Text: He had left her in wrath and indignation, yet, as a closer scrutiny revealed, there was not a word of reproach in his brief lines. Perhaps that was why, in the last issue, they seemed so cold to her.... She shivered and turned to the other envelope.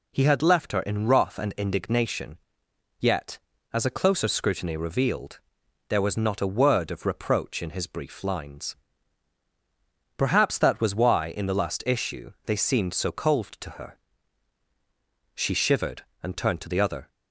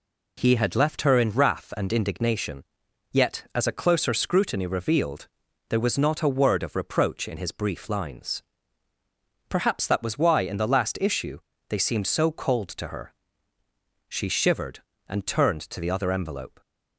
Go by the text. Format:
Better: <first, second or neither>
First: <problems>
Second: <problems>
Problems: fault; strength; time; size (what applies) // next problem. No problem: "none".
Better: second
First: stops before "envelope"; at 17.0 s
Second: none